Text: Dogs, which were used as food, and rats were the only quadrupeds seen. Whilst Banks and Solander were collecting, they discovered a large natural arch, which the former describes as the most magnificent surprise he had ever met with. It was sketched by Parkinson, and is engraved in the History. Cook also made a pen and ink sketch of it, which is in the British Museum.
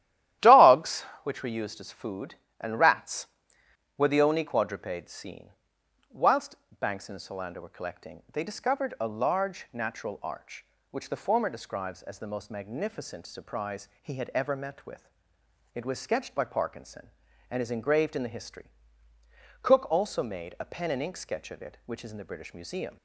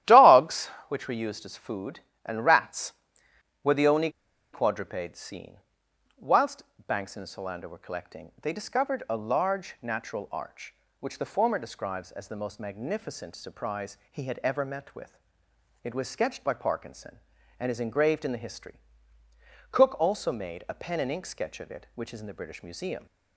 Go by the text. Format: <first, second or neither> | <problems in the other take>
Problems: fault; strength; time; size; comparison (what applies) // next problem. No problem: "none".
first | starts louder than the rest; strong; until 1.2 s; 13 dB; strong in the first // pauses between "only" and "quadrupeds"; at 4.1 s; 0.42 s long // pauses between "Whilst" and "Banks"; slight; at 6.6 s; 0.24 s long; slight in the first